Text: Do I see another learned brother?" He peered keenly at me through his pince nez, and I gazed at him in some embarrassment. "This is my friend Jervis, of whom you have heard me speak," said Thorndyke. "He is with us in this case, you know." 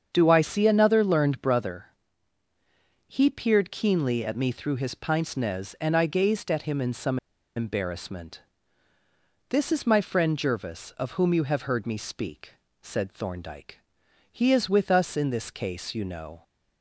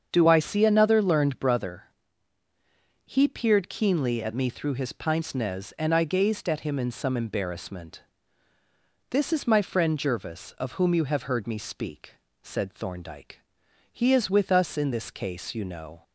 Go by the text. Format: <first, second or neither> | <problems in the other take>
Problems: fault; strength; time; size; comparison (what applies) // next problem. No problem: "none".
second | starts louder than the rest; strong; until 1.1 s; 7.5 dB; strong in the second // pauses between "some" and "embarrassment"; at 7.1 s; 0.38 s long